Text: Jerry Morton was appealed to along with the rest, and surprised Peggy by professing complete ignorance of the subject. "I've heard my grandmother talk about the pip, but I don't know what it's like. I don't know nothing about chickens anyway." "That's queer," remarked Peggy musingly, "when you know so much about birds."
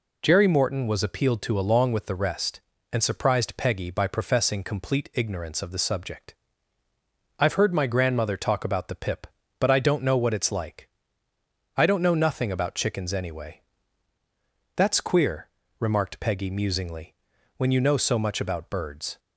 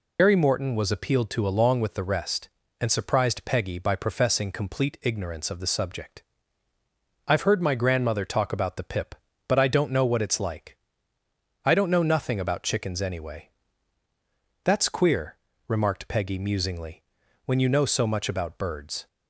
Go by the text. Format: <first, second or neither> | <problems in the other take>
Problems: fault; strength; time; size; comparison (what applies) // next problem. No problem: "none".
first | loses the start of "Jerry"; at 0.1 s; 90 ms